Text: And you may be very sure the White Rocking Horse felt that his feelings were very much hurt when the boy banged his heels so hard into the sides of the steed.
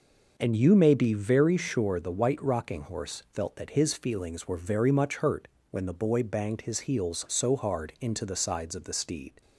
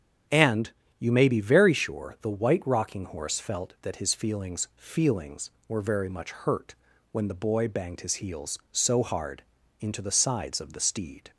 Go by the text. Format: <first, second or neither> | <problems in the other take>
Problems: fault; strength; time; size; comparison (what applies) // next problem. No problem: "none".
first | starts louder than the rest; strong; until 1.5 s; 9 dB // pauses between "And" and "you"; slight; at 0.7 s; 0.28 s long // says "feelings" twice; at 4.7 s // pauses between "hurt" and "when"; at 6.7 s; 0.38 s long; slight in the first // pauses between "hard" and "into"; at 9.4 s; 0.38 s long